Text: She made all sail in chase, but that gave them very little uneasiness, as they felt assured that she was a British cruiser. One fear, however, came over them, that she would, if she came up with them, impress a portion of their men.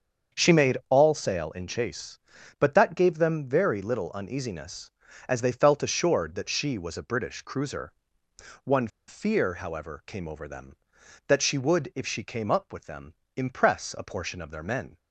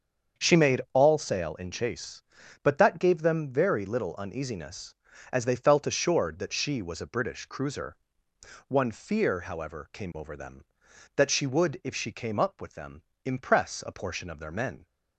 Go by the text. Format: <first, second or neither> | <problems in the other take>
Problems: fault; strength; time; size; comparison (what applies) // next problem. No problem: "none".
second | starts louder than the rest; until 1.4 s; 7 dB; also in the second // pauses between "One" and "fear"; slight; at 8.8 s; 0.19 s long